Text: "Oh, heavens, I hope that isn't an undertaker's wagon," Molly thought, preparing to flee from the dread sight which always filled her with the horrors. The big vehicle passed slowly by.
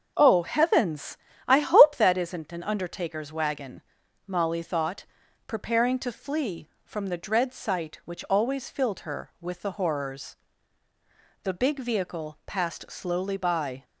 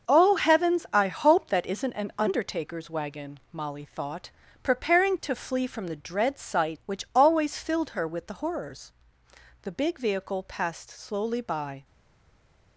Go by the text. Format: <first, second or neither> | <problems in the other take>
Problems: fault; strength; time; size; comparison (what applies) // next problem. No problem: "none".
first | starts louder than the rest; until 1.1 s; 6.5 dB; also in the first // stays silent after the last word; slight; from 11.8 s on; 0.9 s long